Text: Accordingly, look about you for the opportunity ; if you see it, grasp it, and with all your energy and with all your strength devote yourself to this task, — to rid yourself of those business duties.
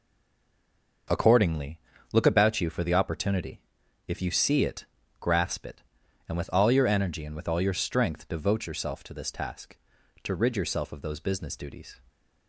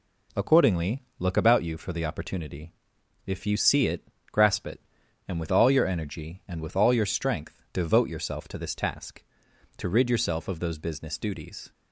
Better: second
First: stays silent before the first word; until 1.0 s; 1.0 s long // starts louder than the rest; noticeable; until 2.4 s; 6 dB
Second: none

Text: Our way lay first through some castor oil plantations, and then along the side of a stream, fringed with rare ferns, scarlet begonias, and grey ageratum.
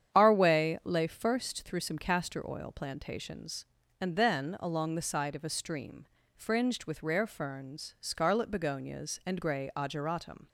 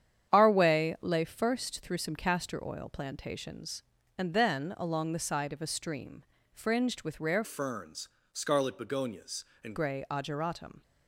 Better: first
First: starts louder than the rest; strong; until 1.1 s; 9 dB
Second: starts louder than the rest; strong; until 1.3 s; 9 dB // changes voice from "ferns" to "and"; from 7.4 to 9.7 s; 2.3 s long

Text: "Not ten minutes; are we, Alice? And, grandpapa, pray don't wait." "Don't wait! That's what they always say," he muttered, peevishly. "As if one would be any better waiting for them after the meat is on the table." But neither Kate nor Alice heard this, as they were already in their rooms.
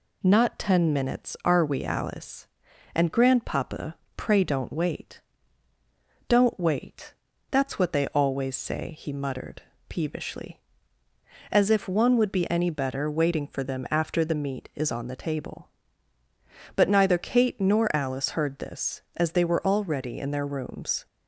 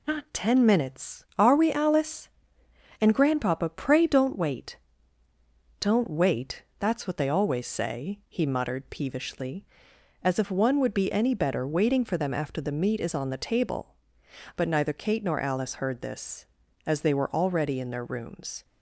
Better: neither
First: none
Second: none

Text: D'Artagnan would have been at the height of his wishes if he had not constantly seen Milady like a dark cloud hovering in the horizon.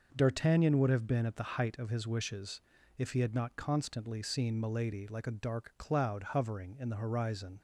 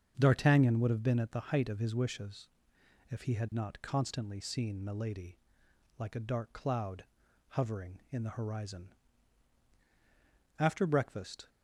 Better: first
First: pauses between "wishes" and "if"; at 2.5 s; 0.38 s long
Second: starts louder than the rest; until 1.1 s; 7 dB // pauses between "wishes" and "if"; noticeable; at 2.4 s; 0.62 s long // pauses between "Milady" and "like"; noticeable; at 5.3 s; 0.58 s long // pauses between "cloud" and "hovering"; at 7.0 s; 0.44 s long // goes on to say "After breakfast"; noticeable; from 10.5 s on; 0.90 s long

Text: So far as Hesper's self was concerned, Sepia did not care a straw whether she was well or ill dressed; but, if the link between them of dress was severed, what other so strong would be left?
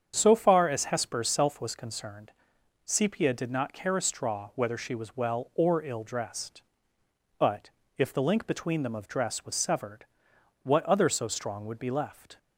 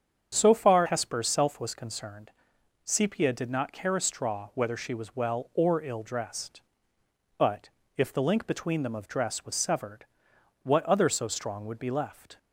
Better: first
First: starts louder than the rest; strong; until 1.1 s; 7.5 dB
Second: starts louder than the rest; strong; until 1.3 s; 8 dB // skips "as"; at 0.8 s

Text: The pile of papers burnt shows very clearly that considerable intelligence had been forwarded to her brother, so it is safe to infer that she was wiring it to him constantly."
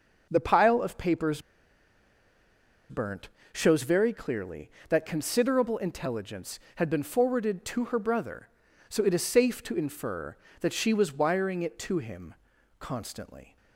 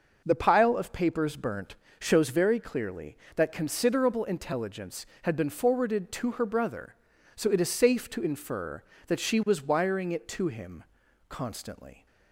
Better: second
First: pauses between "papers" and "burnt"; strong; at 1.3 s; 1.4 s long // pauses between "burnt" and "shows"; slight; at 3.2 s; 0.24 s long // pauses between "him" and "constantly"; at 12.3 s; 0.44 s long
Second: pauses between "burnt" and "shows"; slight; at 1.7 s; 0.24 s long // pauses between "him" and "constantly"; at 10.8 s; 0.44 s long

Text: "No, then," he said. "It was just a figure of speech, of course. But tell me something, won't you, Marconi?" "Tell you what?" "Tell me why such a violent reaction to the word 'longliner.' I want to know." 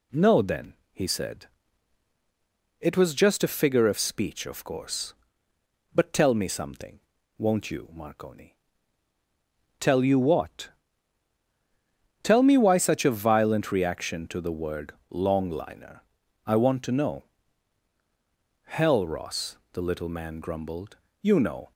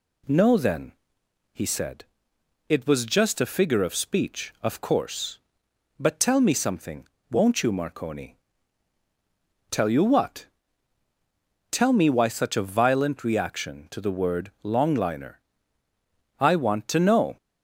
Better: second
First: pauses between "word" and "longliner"; slight; at 14.9 s; 0.16 s long // goes on to say "Hell Ross the little man grumbled you know"; strong; from 18.6 s on; 3.0 s long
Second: none

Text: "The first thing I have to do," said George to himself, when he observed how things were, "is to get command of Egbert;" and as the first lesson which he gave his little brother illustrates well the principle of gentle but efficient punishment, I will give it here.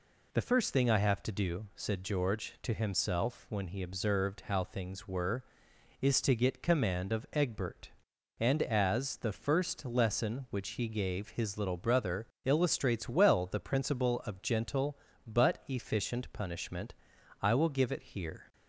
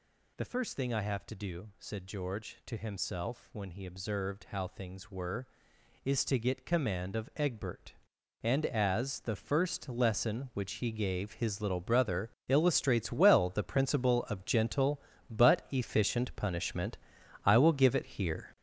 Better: first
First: pauses between "brother" and "illustrates"; slight; at 12.2 s; 0.16 s long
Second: gets louder; strong; throughout; 7 dB // pauses between "brother" and "illustrates"; slight; at 12.3 s; 0.16 s long

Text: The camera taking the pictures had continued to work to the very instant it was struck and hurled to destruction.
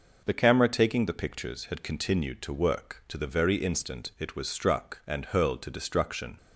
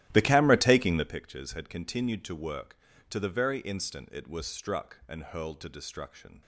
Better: first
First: none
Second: starts louder than the rest; strong; until 1.2 s; 14 dB

